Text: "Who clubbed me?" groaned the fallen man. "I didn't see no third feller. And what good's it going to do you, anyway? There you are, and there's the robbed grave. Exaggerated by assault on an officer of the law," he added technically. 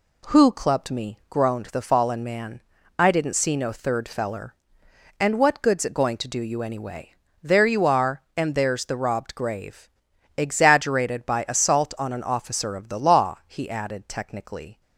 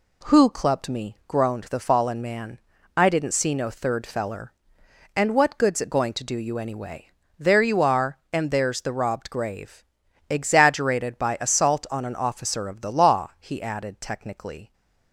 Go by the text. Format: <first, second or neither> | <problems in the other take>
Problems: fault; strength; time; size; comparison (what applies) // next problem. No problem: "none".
neither | none